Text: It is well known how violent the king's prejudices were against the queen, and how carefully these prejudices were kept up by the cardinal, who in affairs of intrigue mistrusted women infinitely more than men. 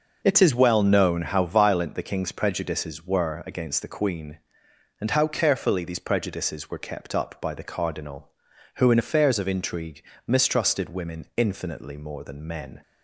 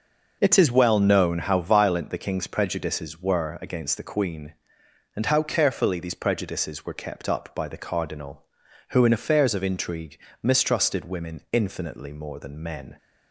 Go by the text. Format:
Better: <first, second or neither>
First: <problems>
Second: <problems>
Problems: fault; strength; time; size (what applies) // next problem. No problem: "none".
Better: neither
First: pauses between "intrigue" and "mistrusted"; slight; at 10.0 s; 0.24 s long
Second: pauses between "intrigue" and "mistrusted"; slight; at 10.1 s; 0.24 s long